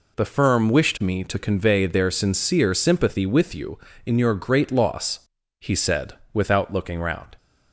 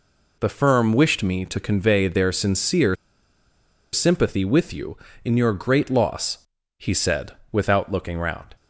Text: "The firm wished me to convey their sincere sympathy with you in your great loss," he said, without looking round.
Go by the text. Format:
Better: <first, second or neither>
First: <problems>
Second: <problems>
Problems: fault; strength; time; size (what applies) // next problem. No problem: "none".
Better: first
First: none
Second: pauses between "sincere" and "sympathy"; at 2.9 s; 0.98 s long